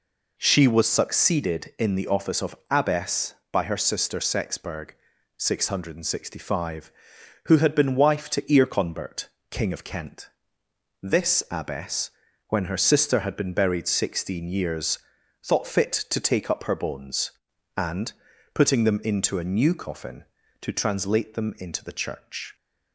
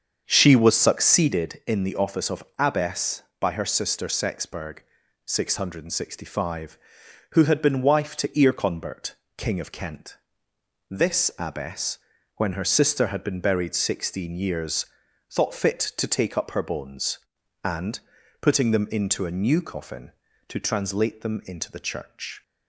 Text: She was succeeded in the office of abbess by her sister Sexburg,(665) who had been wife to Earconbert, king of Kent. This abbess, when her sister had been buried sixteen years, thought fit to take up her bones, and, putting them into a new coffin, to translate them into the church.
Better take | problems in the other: first | starts louder than the rest; strong; until 1.5 s; 7 dB // pauses between "of" and "abbess"; slight; at 2.4 s; 0.16 s long; slight in the first

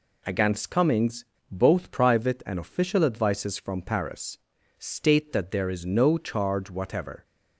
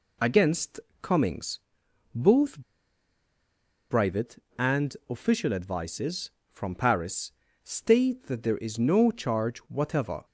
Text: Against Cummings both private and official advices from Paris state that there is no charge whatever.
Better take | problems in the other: first | pauses between "Against" and "Cummings"; slight; at 0.8 s; 0.20 s long // pauses between "Cummings" and "both"; noticeable; at 1.6 s; 0.54 s long; slight in the first // pauses between "both" and "private"; strong; at 2.6 s; 1.3 s long // pauses between "Paris" and "state"; slight; at 7.3 s; 0.32 s long; also in the first

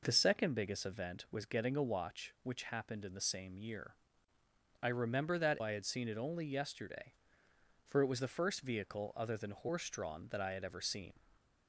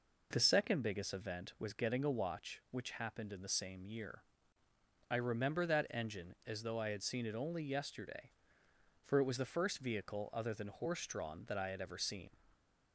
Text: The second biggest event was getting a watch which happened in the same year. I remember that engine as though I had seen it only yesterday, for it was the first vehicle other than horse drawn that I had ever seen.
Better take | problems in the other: second | skips "engine as though"; at 5.6 s

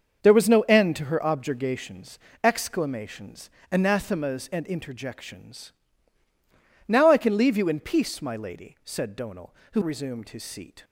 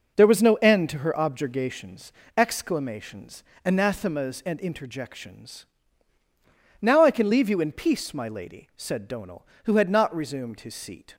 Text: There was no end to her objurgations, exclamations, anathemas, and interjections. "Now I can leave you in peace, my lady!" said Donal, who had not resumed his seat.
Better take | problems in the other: second | starts louder than the rest; until 1.2 s; 6.5 dB // skips "had not"; at 9.8 s

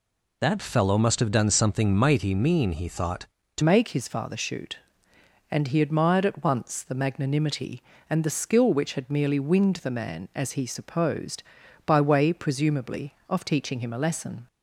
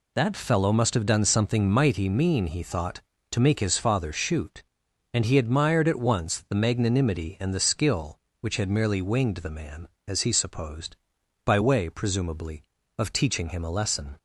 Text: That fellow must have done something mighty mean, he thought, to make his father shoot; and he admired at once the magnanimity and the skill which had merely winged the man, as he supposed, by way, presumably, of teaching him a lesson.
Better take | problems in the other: second | changes voice at "make"; from 3.6 s on; 10.8 s long

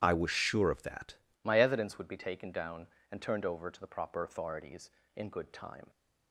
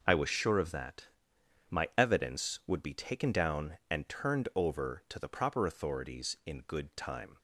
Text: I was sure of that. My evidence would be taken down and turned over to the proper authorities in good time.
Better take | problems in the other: second | starts louder than the rest; strong; until 1.0 s; 10.5 dB // changes voice at "My"; from 1.4 s on; 4.4 s long

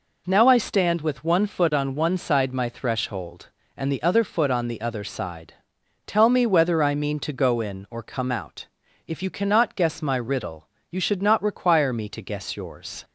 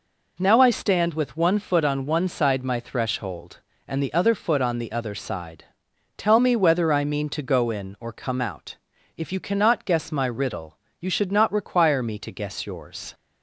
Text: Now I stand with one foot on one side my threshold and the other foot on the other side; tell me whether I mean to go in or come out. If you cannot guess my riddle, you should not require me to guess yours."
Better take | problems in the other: neither | none

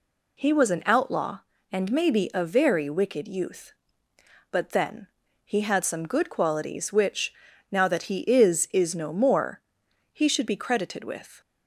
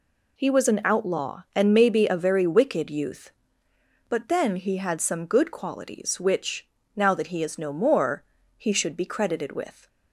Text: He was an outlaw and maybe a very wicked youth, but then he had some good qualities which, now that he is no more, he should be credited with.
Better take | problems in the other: second | pauses between "then" and "he"; slight; at 5.0 s; 0.36 s long // says "is" twice; at 8.7 s

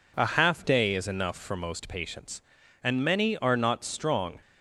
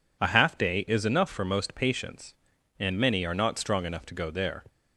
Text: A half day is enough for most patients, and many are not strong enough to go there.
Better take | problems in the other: second | stops before "enough to go there"; at 4.4 s

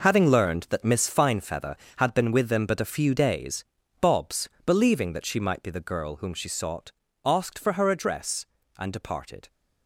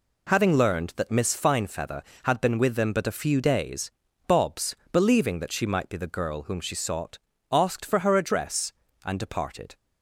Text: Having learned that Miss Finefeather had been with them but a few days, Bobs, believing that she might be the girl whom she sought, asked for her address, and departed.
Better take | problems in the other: second | gets quieter; strong; throughout; 12 dB

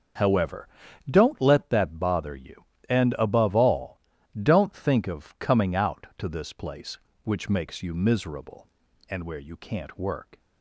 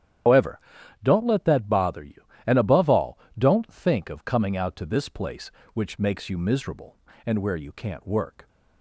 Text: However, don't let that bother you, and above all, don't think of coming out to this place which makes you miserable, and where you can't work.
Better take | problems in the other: first | loses the start of "However"; at 0.2 s; 145 ms // starts louder than the rest; strong; until 1.6 s; 10 dB; also in the first

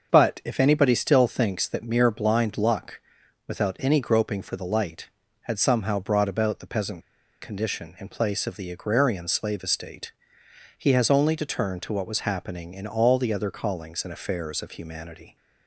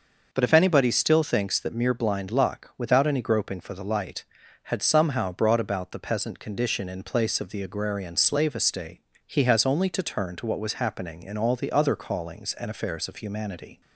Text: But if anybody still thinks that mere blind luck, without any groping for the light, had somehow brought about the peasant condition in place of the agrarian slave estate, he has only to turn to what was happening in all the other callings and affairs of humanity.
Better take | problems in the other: second | starts louder than the rest; until 1.1 s; 6.5 dB // pauses between "peasant" and "condition"; at 7.0 s; 0.40 s long

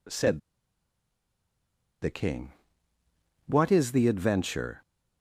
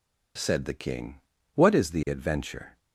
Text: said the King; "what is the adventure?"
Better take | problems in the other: second | pauses between "said" and "the"; strong; at 0.3 s; 1.6 s long

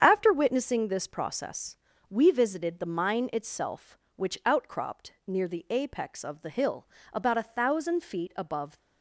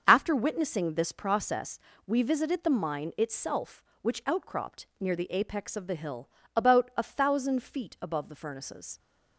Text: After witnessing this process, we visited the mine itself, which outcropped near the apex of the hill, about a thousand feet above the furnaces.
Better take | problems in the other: second | starts louder than the rest; strong; until 1.0 s; 8 dB; also in the second // stops before "the furnaces"; at 8.7 s

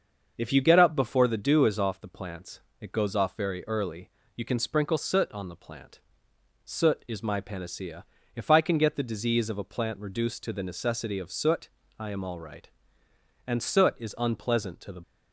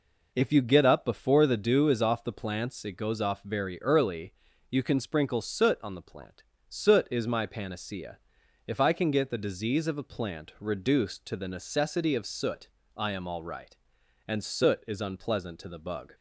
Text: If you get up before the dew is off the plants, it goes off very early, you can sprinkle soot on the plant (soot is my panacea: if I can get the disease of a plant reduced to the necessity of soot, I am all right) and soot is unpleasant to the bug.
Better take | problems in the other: second | starts louder than the rest; until 1.3 s; 6.5 dB // stops before "bug"; at 15.0 s

